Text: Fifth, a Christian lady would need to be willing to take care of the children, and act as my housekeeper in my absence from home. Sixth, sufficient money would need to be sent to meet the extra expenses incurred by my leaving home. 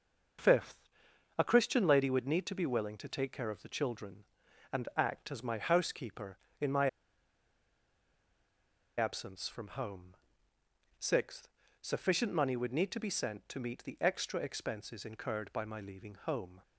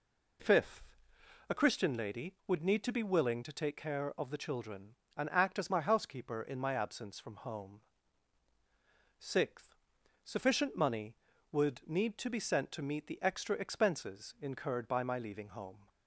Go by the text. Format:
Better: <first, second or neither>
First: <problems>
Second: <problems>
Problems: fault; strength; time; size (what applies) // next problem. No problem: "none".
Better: second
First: pauses between "my" and "absence"; strong; at 6.8 s; 2.1 s long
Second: none